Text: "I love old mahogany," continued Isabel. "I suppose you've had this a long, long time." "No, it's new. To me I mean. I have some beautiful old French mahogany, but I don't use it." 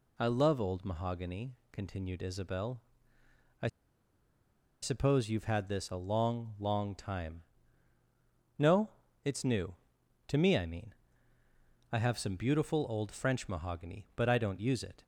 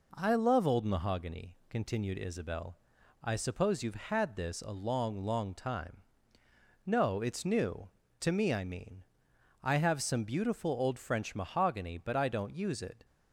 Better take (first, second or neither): second